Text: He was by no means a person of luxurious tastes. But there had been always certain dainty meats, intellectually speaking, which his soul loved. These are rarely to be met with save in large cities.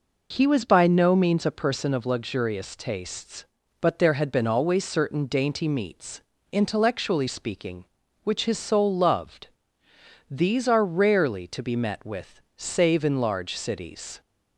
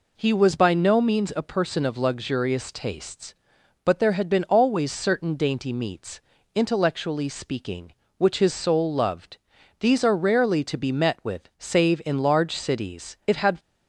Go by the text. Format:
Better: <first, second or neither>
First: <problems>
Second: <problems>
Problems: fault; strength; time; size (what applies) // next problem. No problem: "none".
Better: first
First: none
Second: goes on to say "It had"; slight; from 13.2 s on; 0.32 s long